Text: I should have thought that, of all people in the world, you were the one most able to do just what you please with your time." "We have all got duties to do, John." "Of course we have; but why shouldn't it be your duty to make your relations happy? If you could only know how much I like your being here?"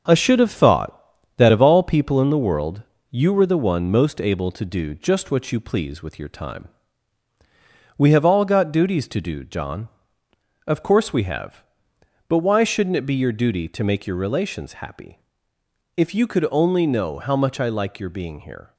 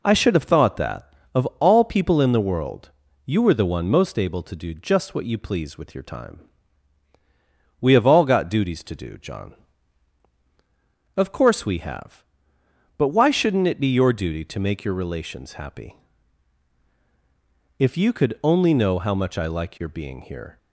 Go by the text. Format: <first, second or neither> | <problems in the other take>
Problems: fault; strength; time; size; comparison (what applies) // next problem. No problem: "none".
second | gets quieter; noticeable; throughout; 5 dB